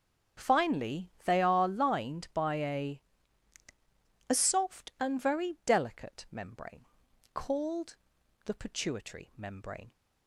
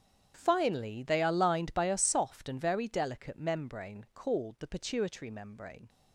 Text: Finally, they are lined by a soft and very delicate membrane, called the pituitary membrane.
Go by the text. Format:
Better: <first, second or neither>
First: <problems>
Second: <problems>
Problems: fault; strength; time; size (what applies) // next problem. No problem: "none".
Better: second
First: starts louder than the rest; strong; until 1.5 s; 7.5 dB // says "a" twice; at 4.2 s // pauses between "called" and "the"; noticeable; at 7.9 s; 0.48 s long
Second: starts louder than the rest; strong; until 1.3 s; 8.5 dB